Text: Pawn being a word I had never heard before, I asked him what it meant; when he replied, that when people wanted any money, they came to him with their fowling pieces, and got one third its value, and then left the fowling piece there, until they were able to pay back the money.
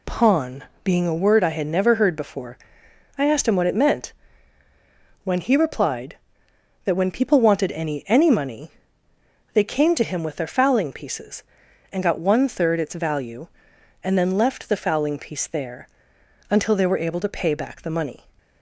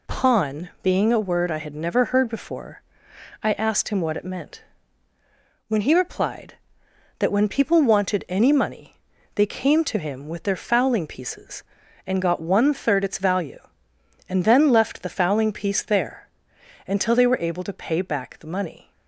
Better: second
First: pauses between "Pawn" and "being"; slight; at 0.6 s; 0.20 s long // says "any" twice; at 8.0 s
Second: none

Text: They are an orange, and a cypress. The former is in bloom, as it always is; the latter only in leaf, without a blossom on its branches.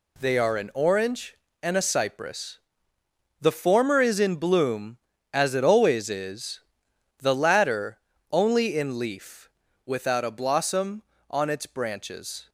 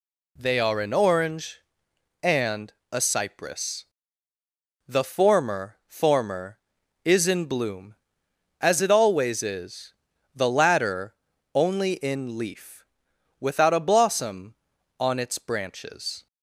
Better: first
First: pauses between "latter" and "only"; slight; at 7.9 s; 0.32 s long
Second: pauses between "and" and "a"; slight; at 2.7 s; 0.22 s long // says "former" twice; at 5.8 s // pauses between "latter" and "only"; at 11.1 s; 0.40 s long

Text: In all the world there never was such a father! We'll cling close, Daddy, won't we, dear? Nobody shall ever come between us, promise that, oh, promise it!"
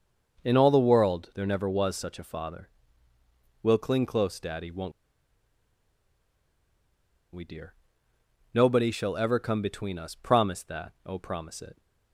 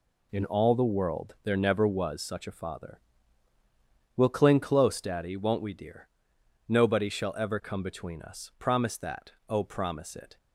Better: second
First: starts louder than the rest; noticeable; until 1.4 s; 6 dB // pauses between "won't" and "we"; strong; at 4.9 s; 2.4 s long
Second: none

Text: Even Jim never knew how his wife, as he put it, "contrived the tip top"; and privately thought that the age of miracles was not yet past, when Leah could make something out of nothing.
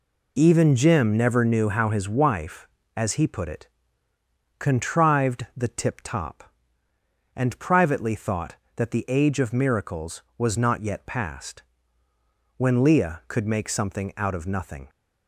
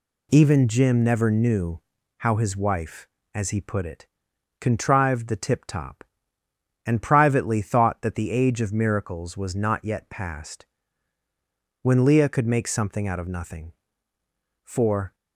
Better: first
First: none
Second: pauses between "knew" and "how"; at 1.8 s; 0.38 s long // goes on to say "For"; from 14.6 s on; 0.50 s long

